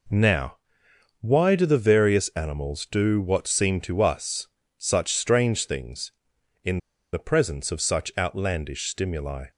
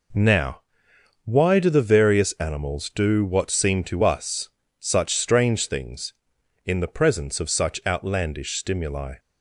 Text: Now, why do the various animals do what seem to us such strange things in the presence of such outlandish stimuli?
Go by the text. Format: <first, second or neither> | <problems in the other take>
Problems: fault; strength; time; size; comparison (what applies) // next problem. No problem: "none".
second | pauses between "us" and "such"; slight; at 4.4 s; 0.30 s long; slight in the second // pauses between "in" and "the"; slight; at 6.7 s; 0.35 s long